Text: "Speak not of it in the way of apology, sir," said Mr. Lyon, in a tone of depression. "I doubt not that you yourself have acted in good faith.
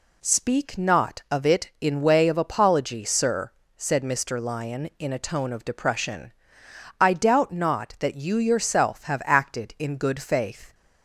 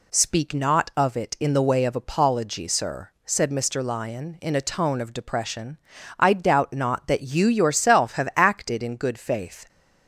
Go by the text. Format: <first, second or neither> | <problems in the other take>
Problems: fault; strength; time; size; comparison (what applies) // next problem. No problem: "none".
second | skips "the"; at 2.0 s